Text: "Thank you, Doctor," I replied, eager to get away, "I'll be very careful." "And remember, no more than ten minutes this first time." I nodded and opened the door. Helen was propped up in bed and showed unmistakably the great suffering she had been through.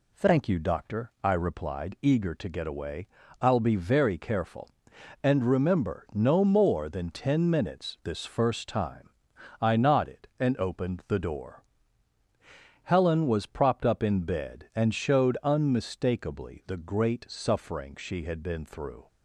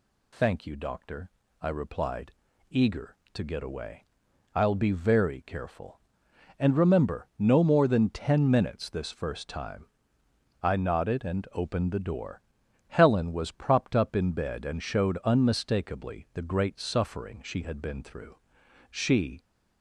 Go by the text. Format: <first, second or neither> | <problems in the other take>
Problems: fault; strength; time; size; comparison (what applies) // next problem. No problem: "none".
first | goes on to say "She"; from 18.8 s on; 0.50 s long